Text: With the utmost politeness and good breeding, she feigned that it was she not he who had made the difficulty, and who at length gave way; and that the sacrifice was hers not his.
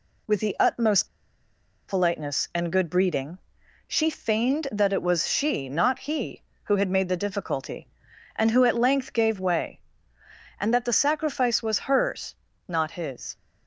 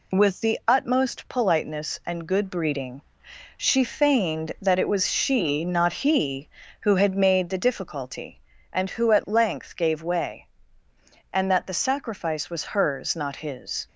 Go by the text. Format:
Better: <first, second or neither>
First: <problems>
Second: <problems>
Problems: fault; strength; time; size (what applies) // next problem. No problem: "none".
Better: second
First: pauses between "utmost" and "politeness"; noticeable; at 1.0 s; 0.80 s long // pauses between "hers" and "not"; slight; at 12.3 s; 0.32 s long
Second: none